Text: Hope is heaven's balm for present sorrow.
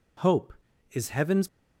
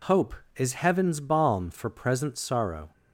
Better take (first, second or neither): second